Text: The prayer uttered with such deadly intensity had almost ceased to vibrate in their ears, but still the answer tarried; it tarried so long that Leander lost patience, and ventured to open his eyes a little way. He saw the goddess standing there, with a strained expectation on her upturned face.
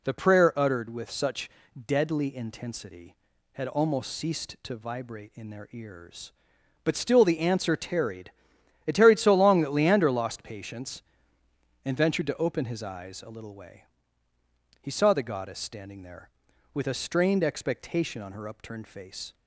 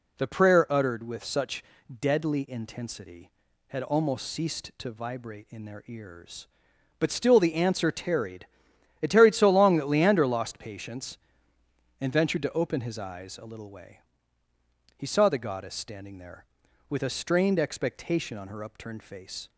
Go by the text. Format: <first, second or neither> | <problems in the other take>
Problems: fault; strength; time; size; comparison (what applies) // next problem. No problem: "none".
neither | pauses between "such" and "deadly"; the same in both